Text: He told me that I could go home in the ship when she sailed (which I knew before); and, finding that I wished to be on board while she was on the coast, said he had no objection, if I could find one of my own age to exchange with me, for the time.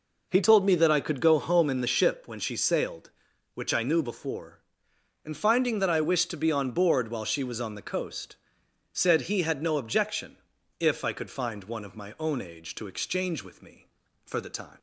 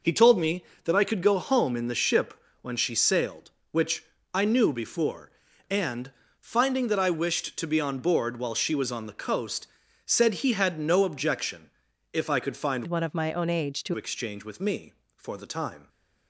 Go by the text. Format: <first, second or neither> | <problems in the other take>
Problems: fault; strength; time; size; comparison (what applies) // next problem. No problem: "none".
first | pauses between "ship" and "when"; slight; at 2.3 s; 0.28 s long // pauses between "which" and "I"; slight; at 4.0 s; 0.28 s long // changes voice from "one" to "to"; from 12.8 to 13.9 s; 1.1 s long